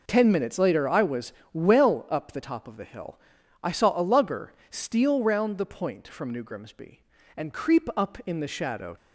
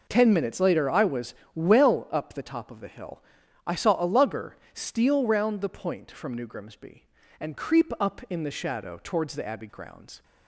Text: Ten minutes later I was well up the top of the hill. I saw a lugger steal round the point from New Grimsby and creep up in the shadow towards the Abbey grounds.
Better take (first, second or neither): second